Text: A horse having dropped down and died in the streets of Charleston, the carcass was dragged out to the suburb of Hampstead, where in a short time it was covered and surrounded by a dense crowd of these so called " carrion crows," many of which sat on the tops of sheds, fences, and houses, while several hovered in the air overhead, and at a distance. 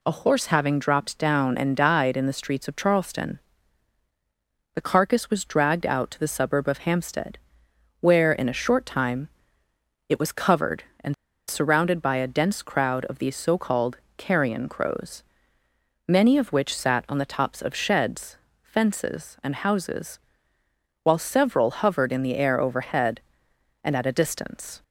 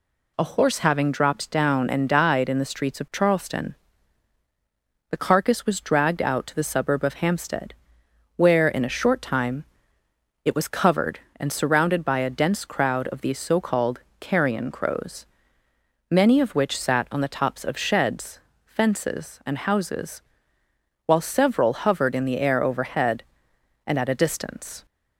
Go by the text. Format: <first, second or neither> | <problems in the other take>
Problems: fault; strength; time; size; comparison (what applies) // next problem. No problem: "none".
second | pauses between "time" and "it"; noticeable; at 9.2 s; 0.80 s long; noticeable in the second // pauses between "and" and "surrounded"; slight; at 11.1 s; 0.33 s long